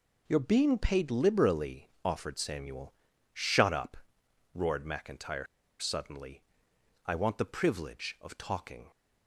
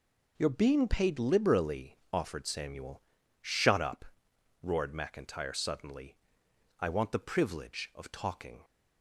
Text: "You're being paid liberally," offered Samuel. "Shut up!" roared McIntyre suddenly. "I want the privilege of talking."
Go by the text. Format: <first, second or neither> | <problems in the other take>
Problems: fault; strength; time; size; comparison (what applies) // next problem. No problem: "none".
second | pauses between "McIntyre" and "suddenly"; slight; at 5.4 s; 0.34 s long